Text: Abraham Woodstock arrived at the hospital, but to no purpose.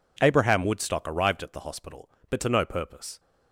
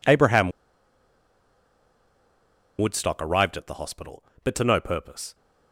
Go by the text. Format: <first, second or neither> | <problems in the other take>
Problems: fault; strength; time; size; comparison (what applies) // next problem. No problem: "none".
first | pauses between "Abraham" and "Woodstock"; strong; at 0.5 s; 2.2 s long